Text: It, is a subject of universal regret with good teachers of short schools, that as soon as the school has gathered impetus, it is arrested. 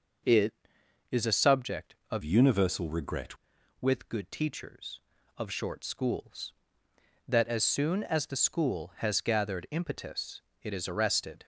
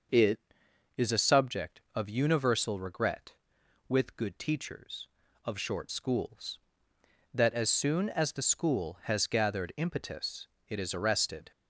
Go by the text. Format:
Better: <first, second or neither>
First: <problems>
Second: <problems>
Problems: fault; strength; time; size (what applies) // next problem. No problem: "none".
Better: second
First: starts louder than the rest; until 1.8 s; 6 dB // changes voice from "universal" to "regret"; from 2.2 to 3.3 s; 1.1 s long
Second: starts louder than the rest; until 1.6 s; 6 dB